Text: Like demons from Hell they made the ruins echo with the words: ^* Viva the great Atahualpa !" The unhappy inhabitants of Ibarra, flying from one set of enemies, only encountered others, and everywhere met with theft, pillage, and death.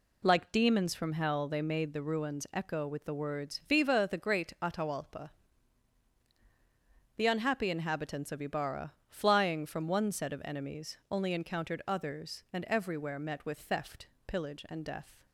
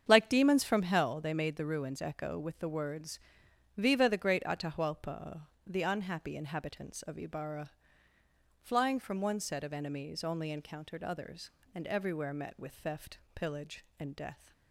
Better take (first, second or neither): first